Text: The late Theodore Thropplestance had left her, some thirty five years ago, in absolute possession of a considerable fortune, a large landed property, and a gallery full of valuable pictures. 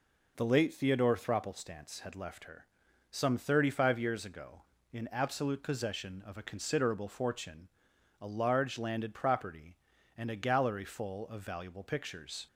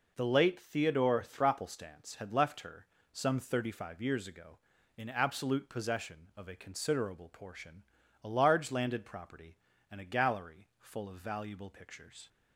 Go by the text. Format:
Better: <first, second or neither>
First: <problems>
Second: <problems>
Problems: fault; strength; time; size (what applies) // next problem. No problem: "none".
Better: first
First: none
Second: says "portion" for "fortune"; at 7.3 s